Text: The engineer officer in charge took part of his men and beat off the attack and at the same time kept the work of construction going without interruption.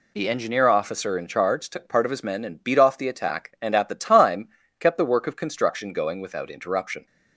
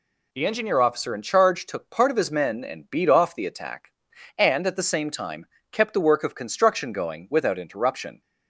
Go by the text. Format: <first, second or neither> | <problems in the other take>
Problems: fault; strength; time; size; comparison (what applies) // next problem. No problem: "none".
second | skips "same"; at 3.9 s // pauses between "time" and "kept"; slight; at 4.4 s; 0.32 s long; slight in the second